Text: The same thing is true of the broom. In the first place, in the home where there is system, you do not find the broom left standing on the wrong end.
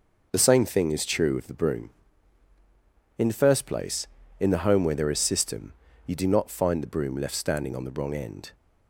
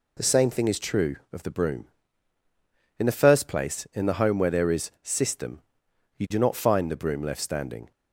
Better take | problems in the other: first | stops before "on the wrong end"; at 7.9 s

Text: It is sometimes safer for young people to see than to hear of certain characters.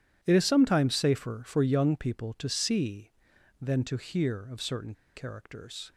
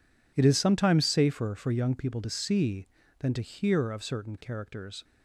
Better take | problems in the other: second | pauses between "certain" and "characters"; slight; at 4.9 s; 0.22 s long

